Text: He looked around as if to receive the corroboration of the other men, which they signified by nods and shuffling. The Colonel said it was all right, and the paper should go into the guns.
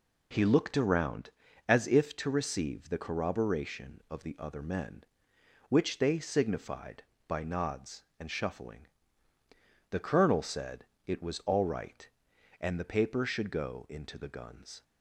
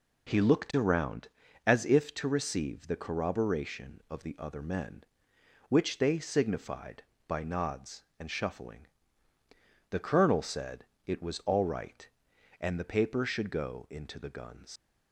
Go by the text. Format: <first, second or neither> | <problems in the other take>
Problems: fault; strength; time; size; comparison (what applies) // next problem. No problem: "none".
first | pauses between "said" and "it"; slight; at 10.8 s; 0.22 s long; slight in the first // leaves "guns" unfinished; at 14.7 s; 80 ms